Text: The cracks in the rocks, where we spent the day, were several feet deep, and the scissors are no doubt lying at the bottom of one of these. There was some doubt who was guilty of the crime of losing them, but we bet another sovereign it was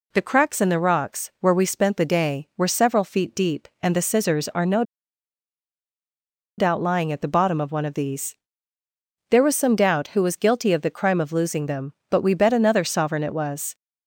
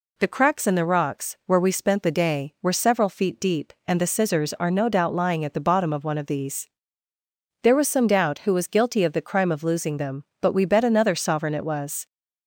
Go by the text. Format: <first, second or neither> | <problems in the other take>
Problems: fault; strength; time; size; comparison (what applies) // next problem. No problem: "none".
second | pauses between "no" and "doubt"; strong; at 4.8 s; 1.7 s long